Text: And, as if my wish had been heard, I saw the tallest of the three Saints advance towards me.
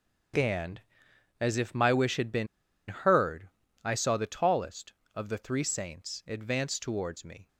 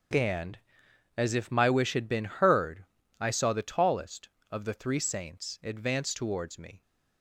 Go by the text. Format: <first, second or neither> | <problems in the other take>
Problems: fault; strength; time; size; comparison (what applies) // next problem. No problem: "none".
second | starts louder than the rest; strong; until 1.9 s; 7 dB; strong in the second // pauses between "been" and "heard"; at 2.4 s; 0.42 s long